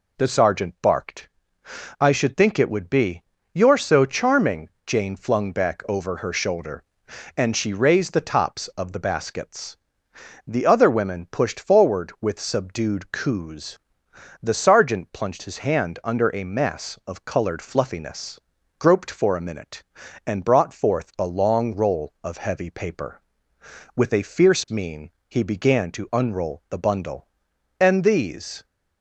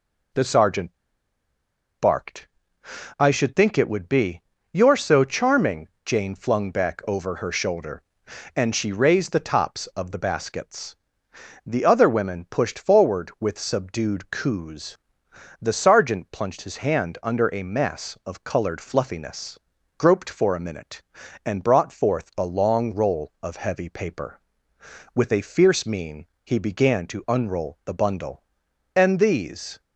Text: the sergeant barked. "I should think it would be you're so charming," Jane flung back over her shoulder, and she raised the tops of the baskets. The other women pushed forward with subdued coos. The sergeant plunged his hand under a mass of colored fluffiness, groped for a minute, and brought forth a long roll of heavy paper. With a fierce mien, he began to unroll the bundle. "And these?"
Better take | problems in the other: first | pauses between "sergeant" and "barked"; at 0.9 s; 1.0 s long // pauses between "be" and "you're"; slight; at 4.4 s; 0.32 s long; slight in the first

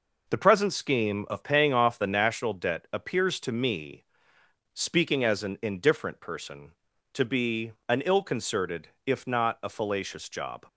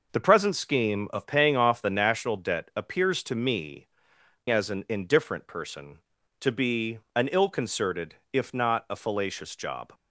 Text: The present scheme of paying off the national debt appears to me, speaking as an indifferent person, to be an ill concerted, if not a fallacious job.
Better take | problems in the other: first | skips "speaking"; at 4.1 s // pauses between "be" and "an"; slight; at 6.9 s; 0.16 s long; slight in the first

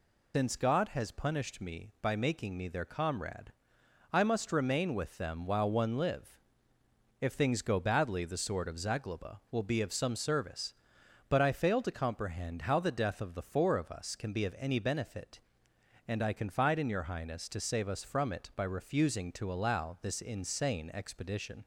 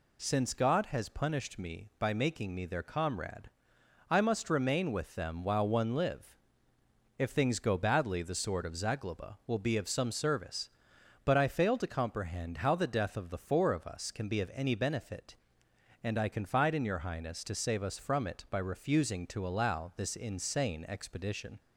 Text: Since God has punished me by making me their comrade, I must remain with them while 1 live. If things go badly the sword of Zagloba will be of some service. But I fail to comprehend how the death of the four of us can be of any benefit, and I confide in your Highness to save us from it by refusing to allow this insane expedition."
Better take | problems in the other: second | loses the start of "Since"; at 0.3 s; 125 ms

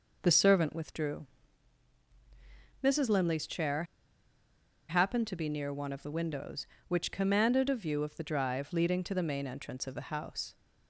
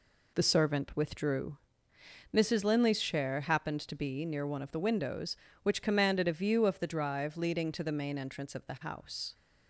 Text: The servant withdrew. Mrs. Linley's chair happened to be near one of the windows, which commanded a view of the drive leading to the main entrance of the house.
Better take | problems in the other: second | pauses between "chair" and "happened"; at 3.8 s; 1.0 s long

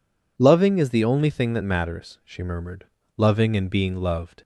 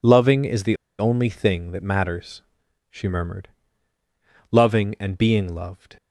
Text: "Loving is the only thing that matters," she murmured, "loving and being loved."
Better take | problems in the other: first | pauses between "the" and "only"; slight; at 0.7 s; 0.23 s long

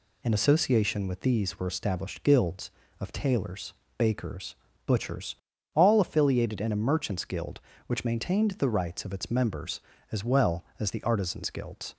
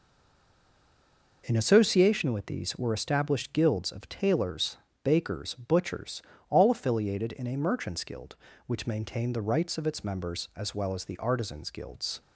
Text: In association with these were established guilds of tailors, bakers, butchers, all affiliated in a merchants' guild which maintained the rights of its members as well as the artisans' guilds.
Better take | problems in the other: first | stays silent before the first word; noticeable; until 1.4 s; 1.4 s long

